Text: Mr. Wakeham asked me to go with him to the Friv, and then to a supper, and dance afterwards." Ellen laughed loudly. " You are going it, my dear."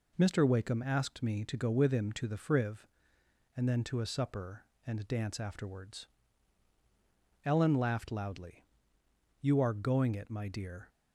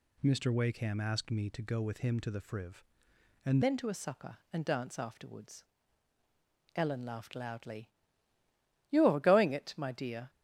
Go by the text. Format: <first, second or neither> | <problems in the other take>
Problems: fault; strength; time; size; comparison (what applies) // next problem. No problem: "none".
first | changes voice at "then"; from 3.6 s on; 6.6 s long